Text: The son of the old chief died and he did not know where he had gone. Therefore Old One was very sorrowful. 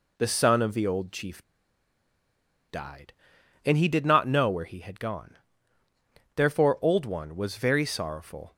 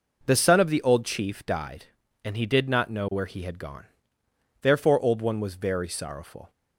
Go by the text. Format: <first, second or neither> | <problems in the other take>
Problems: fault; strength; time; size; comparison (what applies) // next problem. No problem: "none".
second | pauses between "chief" and "died"; strong; at 1.4 s; 1.2 s long